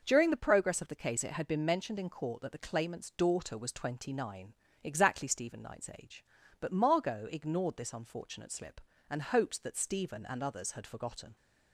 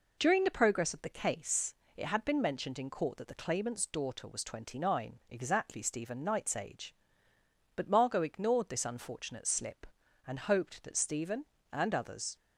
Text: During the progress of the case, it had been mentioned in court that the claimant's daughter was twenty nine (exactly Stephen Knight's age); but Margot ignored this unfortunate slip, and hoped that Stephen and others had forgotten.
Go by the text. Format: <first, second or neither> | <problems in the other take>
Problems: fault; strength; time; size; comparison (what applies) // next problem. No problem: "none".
first | stops before "had forgotten"; at 12.3 s